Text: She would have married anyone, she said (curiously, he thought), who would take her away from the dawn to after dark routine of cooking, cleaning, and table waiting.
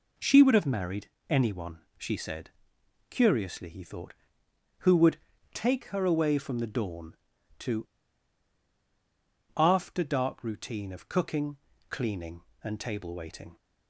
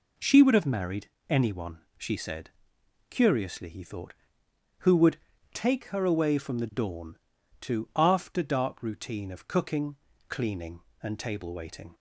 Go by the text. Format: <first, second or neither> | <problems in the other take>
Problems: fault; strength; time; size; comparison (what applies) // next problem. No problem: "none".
second | pauses between "married" and "anyone"; slight; at 1.0 s; 0.20 s long; slight in the second // pauses between "would" and "take"; slight; at 5.1 s; 0.36 s long; slight in the second // pauses between "to" and "after"; strong; at 7.8 s; 1.6 s long